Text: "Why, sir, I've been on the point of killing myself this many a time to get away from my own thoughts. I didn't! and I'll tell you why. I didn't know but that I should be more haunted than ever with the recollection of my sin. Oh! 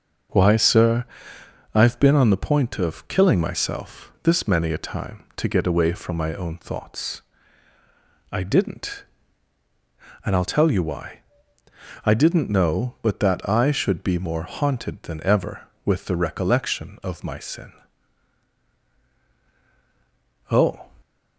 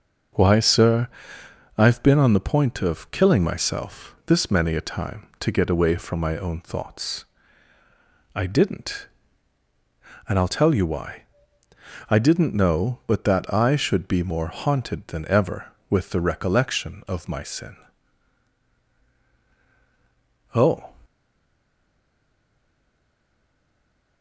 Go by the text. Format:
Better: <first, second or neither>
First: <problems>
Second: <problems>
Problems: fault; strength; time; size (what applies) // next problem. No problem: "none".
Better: first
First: starts louder than the rest; noticeable; until 2.0 s; 6 dB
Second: starts louder than the rest; noticeable; until 2.0 s; 6 dB // stays silent after the last word; strong; from 21.0 s on; 3.2 s long